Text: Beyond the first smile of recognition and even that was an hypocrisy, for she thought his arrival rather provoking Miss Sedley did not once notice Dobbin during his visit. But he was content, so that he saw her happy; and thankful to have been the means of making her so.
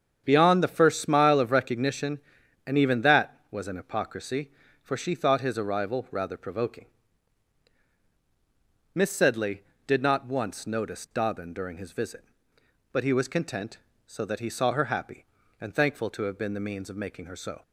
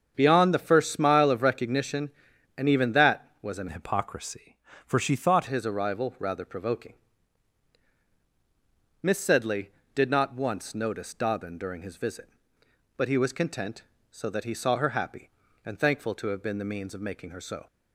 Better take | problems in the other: first | starts louder than the rest; strong; until 1.1 s; 7 dB; strong in the first // changes voice from "hypocrisy" to "thought"; from 3.6 to 5.4 s; 1.8 s long // pauses between "provoking" and "Miss"; strong; at 6.9 s; 2.1 s long; strong in the first

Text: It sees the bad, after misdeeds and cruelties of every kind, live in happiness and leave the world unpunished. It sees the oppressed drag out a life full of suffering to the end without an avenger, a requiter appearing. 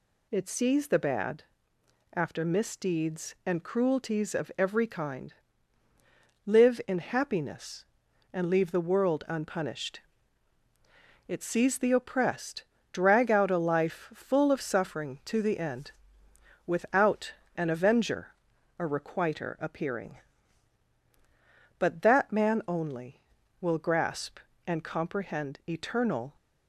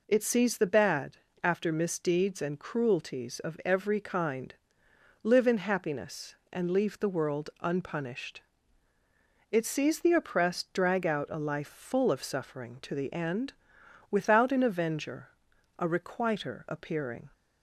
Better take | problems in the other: second | pauses between "oppressed" and "drag"; slight; at 12.6 s; 0.26 s long // pauses between "end" and "without"; noticeable; at 15.9 s; 0.74 s long; noticeable in the second // pauses between "without" and "an"; slight; at 17.3 s; 0.24 s long // goes on to say "But that man only will grasp and comprehend eternal"; strong; from 21.7 s on; 4.5 s long

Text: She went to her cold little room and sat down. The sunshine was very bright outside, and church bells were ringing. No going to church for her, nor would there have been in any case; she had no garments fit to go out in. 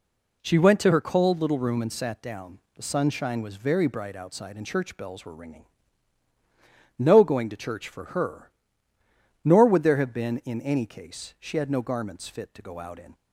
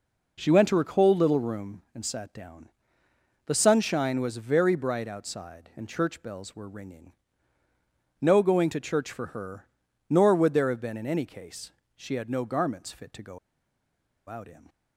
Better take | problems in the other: first | pauses between "go" and "out"; noticeable; at 13.3 s; 0.90 s long

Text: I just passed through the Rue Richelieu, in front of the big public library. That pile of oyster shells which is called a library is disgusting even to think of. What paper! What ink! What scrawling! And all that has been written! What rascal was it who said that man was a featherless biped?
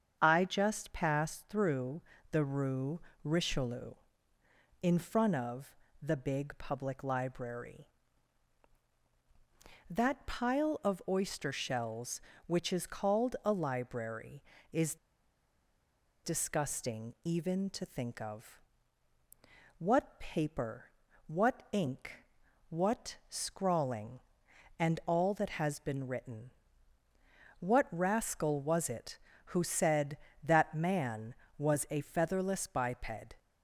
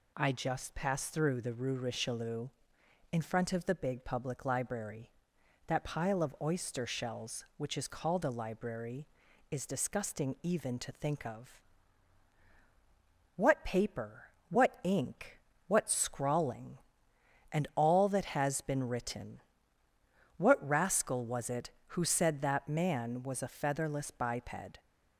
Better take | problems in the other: second | starts louder than the rest; strong; until 1.2 s; 7.5 dB // pauses between "through" and "the"; slight; at 2.0 s; 0.30 s long // pauses between "Rue" and "Richelieu"; slight; at 2.9 s; 0.22 s long // pauses between "of" and "the"; slight; at 5.7 s; 0.26 s long // pauses between "is" and "disgusting"; strong; at 14.9 s; 1.2 s long

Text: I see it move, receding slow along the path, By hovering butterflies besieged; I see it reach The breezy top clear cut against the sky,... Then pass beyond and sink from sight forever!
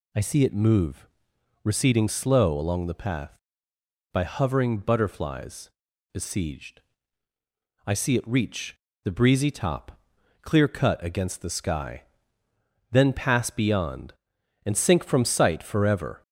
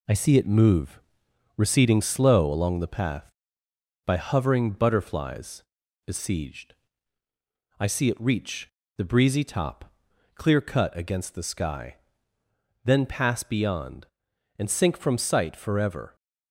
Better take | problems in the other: first | gets quieter; throughout; 3.5 dB // pauses between "butterflies" and "besieged"; at 5.6 s; 0.42 s long; also in the first // pauses between "reach" and "The"; slight; at 8.6 s; 0.28 s long; slight in the first // pauses between "top" and "clear"; at 9.9 s; 0.44 s long; also in the first

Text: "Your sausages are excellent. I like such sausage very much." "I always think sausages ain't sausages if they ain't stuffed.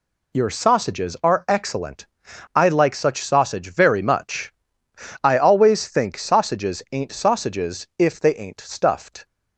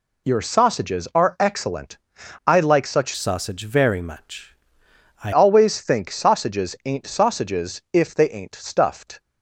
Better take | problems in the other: first | changes voice from "sausage" to "I"; from 3.1 to 5.3 s; 2.2 s long

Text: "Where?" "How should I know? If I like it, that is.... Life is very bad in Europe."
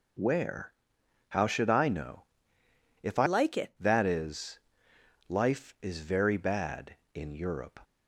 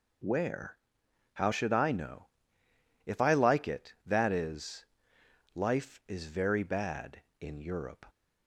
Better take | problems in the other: second | changes voice from "like" to "it"; from 3.2 to 3.7 s; 0.5 s long

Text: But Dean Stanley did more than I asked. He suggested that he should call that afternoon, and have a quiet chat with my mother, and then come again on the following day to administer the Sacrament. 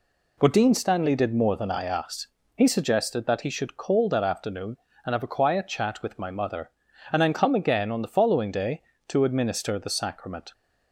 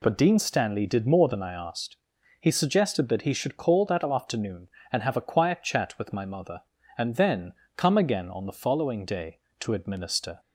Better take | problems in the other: first | pauses between "then" and "come"; slight; at 7.5 s; 0.24 s long // stops before "the Sacrament"; at 10.3 s

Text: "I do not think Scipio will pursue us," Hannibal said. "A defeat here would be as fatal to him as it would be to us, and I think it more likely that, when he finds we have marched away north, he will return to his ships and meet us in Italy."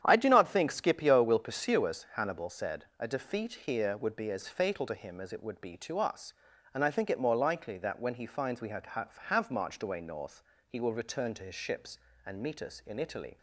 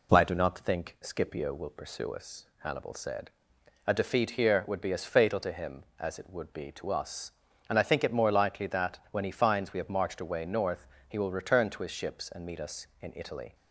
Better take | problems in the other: second | starts louder than the rest; strong; until 1.0 s; 9.5 dB // says "have" twice; at 8.8 s

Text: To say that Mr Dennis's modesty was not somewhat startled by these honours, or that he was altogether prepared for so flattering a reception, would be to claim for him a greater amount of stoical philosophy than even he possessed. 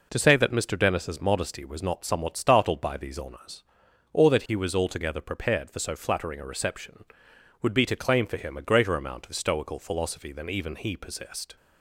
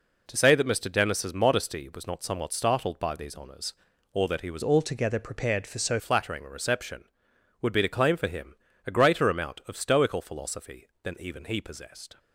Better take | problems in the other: first | changes voice from "altogether" to "so"; from 4.6 to 5.9 s; 1.3 s long // pauses between "him" and "a"; slight; at 8.5 s; 0.32 s long

